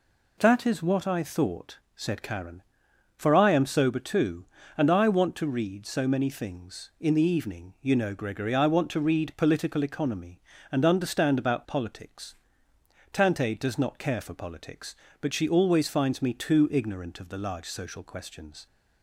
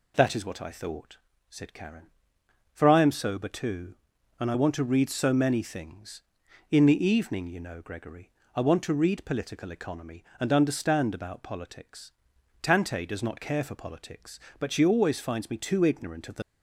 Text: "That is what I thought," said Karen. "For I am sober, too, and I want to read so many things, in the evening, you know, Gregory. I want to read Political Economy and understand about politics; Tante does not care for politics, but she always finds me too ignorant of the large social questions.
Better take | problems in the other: first | stops before "large social questions"; at 16.4 s

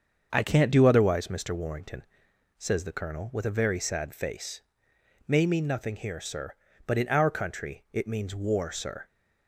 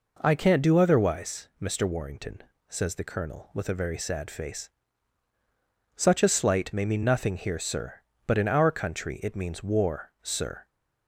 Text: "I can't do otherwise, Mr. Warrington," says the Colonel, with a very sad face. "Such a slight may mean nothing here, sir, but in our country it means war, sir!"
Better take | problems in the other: second | starts louder than the rest; until 1.3 s; 7 dB // skips "Such a slight"; at 4.9 s

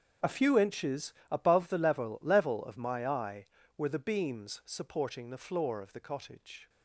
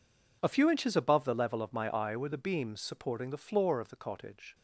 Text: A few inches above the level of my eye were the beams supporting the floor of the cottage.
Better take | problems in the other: second | starts louder than the rest; strong; until 1.3 s; 7.5 dB // pauses between "inches" and "above"; slight; at 1.1 s; 0.16 s long // says "level" twice; at 2.2 s

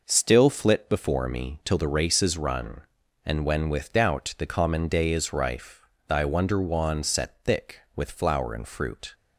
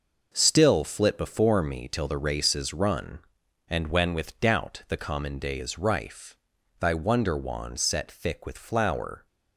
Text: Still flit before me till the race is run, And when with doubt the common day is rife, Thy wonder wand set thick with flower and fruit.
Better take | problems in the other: first | stops before "and fruit"; at 9.2 s

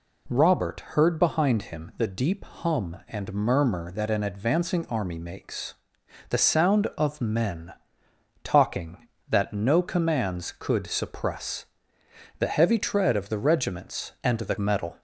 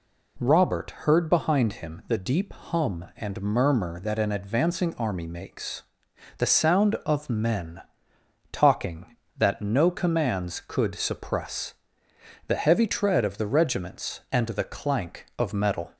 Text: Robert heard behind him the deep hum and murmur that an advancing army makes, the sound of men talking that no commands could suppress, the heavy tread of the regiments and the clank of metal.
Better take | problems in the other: second | pauses between "men" and "talking"; noticeable; at 7.7 s; 0.72 s long; noticeable in the second // skips "clank of"; at 14.5 s

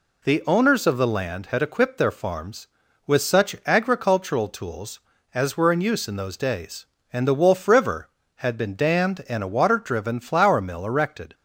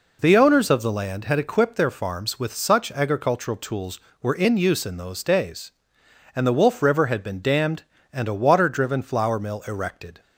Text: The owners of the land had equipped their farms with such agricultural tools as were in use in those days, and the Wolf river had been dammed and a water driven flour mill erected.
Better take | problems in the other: first | skips "as"; at 4.1 s

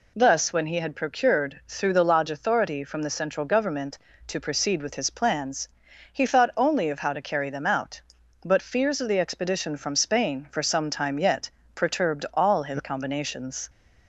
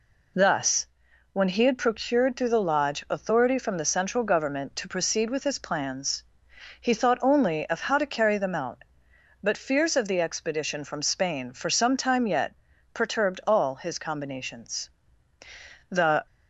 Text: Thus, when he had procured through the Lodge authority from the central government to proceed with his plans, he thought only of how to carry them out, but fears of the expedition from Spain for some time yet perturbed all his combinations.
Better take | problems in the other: first | pauses between "yet" and "perturbed"; at 12.5 s; 0.42 s long; slight in the first // goes on to say "The"; slight; from 15.8 s on; 0.36 s long

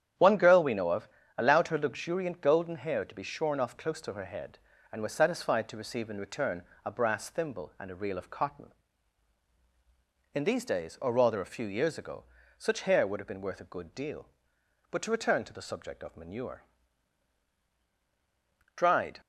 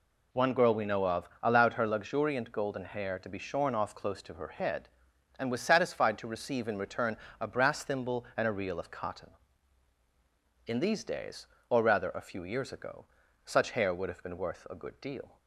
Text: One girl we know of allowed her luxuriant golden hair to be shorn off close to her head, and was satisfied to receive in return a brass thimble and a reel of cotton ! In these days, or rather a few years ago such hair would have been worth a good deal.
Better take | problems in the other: second | starts louder than the rest; strong; until 1.4 s; 9.5 dB // pauses between "of" and "allowed"; slight; at 1.0 s; 0.30 s long; slight in the second // pauses between "return" and "a"; slight; at 6.6 s; 0.20 s long; slight in the second // pauses between "ago" and "such"; slight; at 12.2 s; 0.34 s long; also in the second // goes on to say "But to return to the subject of manure Dried"; strong; from 14.8 s on; 4.3 s long

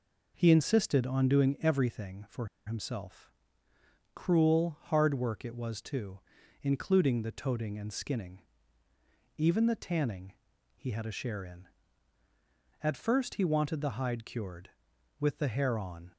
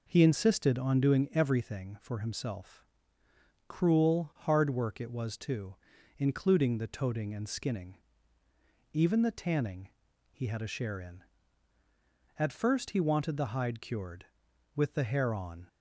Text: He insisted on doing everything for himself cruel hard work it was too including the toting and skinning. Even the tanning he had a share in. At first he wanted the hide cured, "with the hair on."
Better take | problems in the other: second | pauses between "for" and "himself"; slight; at 2.4 s; 0.19 s long // pauses between "himself" and "cruel"; noticeable; at 3.3 s; 0.82 s long; noticeable in the second // pauses between "too" and "including"; at 6.1 s; 0.42 s long; also in the second // pauses between "tanning" and "he"; at 10.3 s; 0.44 s long; also in the second

